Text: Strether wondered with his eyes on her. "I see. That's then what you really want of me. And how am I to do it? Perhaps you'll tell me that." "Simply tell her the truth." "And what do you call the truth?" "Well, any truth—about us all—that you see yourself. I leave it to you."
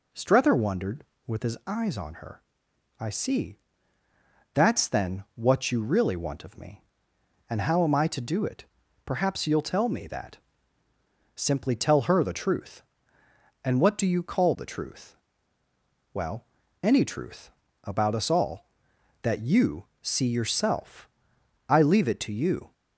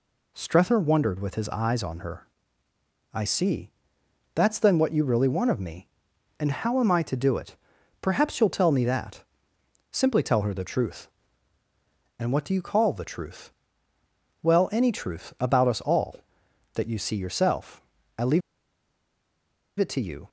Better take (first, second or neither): first